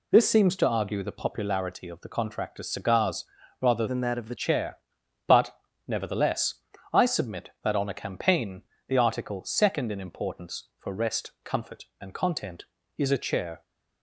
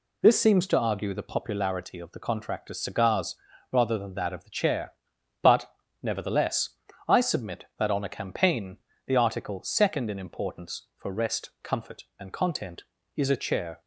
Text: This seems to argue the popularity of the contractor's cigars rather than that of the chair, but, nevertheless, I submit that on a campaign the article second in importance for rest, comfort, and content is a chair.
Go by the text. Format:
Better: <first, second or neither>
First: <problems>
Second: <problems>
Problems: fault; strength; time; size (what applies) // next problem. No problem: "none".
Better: second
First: pauses between "cigars" and "rather"; slight; at 3.2 s; 0.36 s long // changes voice from "than" to "the"; from 3.8 to 4.3 s; 0.5 s long // pauses between "campaign" and "the"; slight; at 8.6 s; 0.26 s long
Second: pauses between "cigars" and "rather"; slight; at 3.3 s; 0.36 s long // pauses between "campaign" and "the"; slight; at 8.7 s; 0.29 s long